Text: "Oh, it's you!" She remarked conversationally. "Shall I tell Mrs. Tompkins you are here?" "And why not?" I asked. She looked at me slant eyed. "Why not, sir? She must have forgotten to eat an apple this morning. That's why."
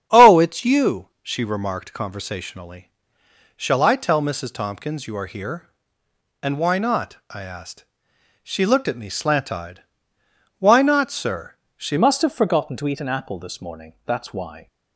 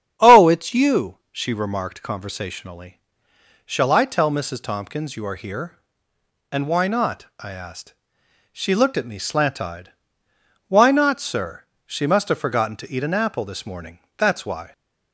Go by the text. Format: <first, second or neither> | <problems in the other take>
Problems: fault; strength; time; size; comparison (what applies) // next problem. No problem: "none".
second | starts louder than the rest; strong; until 1.2 s; 8.5 dB; strong in the second // changes voice at "must"; from 11.9 s on; 2.7 s long